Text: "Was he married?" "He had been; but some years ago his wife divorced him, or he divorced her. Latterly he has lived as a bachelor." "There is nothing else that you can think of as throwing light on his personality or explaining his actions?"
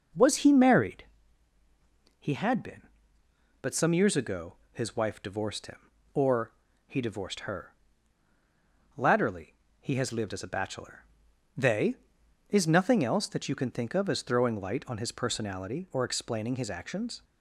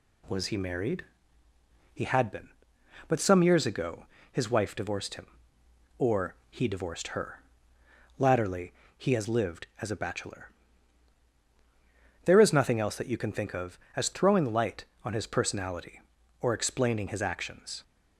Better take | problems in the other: second | pauses between "ago" and "his"; slight; at 4.5 s; 0.16 s long; slight in the second // pauses between "or" and "he"; slight; at 6.5 s; 0.34 s long // pauses between "Latterly" and "he"; slight; at 9.5 s; 0.26 s long; slight in the second // says "They" for "There"; at 11.5 s

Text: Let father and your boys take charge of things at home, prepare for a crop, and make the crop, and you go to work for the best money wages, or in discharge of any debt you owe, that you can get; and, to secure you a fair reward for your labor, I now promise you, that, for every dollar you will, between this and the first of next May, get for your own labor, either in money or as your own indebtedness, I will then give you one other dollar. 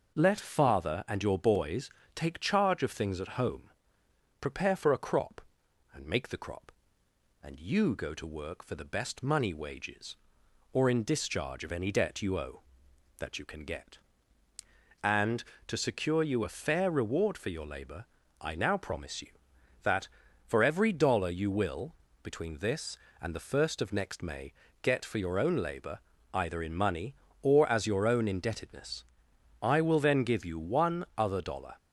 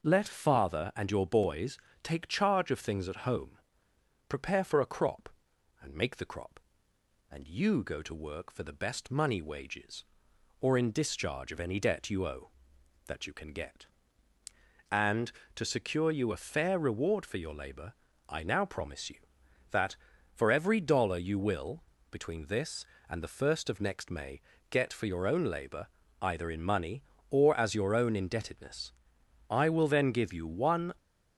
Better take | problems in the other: first | pauses between "boys" and "take"; slight; at 1.7 s; 0.26 s long; slight in the first // stops before "other dollar"; at 30.9 s

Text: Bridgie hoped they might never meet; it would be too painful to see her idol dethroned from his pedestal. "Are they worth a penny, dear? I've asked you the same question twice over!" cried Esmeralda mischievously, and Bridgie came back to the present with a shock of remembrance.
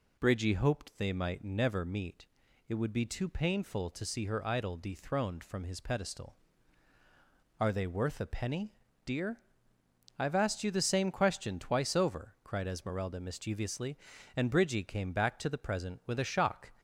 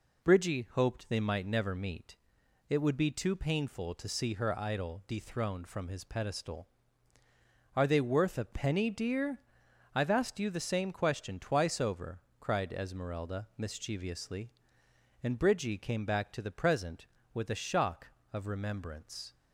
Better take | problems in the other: second | stops before "of remembrance"; at 16.7 s

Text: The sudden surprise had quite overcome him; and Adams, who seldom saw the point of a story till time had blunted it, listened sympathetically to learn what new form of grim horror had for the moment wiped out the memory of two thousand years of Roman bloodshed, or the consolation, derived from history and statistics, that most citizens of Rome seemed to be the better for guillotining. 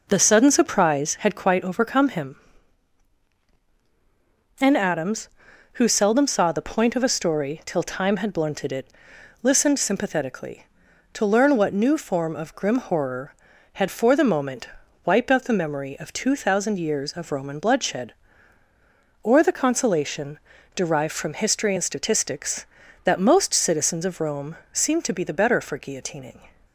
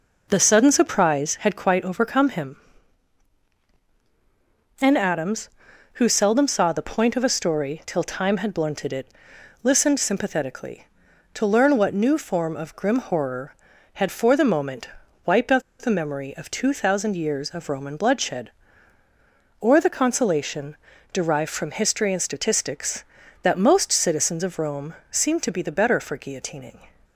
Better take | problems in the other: first | pauses between "moment" and "wiped"; slight; at 14.8 s; 0.36 s long; slight in the first // pauses between "out" and "the"; slight; at 15.6 s; 0.19 s long // pauses between "Rome" and "seemed"; slight; at 24.9 s; 0.16 s long; slight in the first

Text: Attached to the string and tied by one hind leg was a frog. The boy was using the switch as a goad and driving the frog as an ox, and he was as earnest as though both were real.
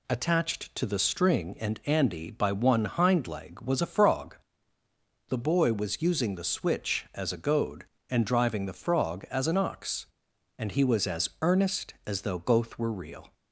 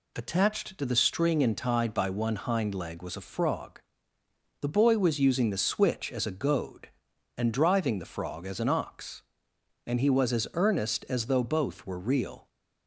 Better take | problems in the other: second | says "andy" for "tied"; at 1.8 s

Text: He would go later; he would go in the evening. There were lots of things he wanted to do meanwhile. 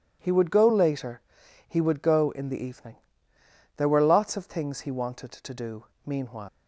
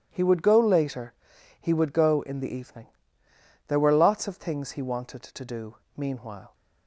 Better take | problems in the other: second | pauses between "do" and "meanwhile"; slight; at 5.8 s; 0.20 s long; slight in the second // leaves "meanwhile" unfinished; at 6.4 s; 140 ms

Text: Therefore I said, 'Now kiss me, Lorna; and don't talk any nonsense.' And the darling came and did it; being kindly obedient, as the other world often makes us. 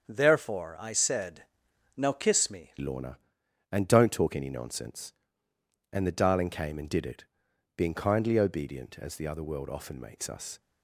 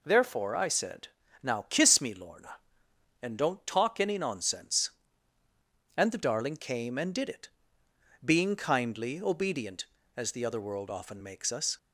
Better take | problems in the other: second | starts louder than the rest; until 1.1 s; 7 dB // changes voice at "Lorna"; from 2.7 s on; 7.8 s long

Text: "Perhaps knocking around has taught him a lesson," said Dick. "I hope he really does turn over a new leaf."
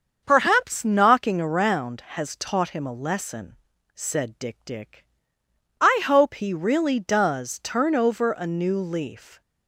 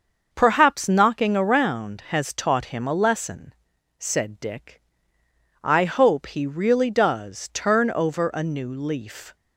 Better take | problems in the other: second | starts louder than the rest; until 1.2 s; 6.5 dB; also in the second // says "Dick" twice; at 4.6 s

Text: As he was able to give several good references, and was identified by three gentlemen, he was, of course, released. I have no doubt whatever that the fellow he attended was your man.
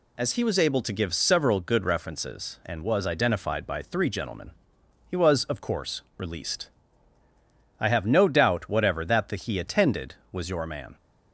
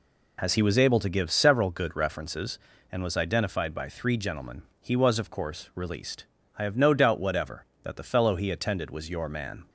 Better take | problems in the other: second | skips "fellow"; at 9.3 s

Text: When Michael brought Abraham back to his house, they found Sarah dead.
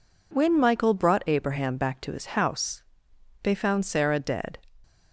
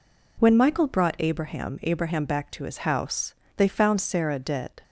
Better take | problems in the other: first | says "Abraham" twice; at 1.8 s

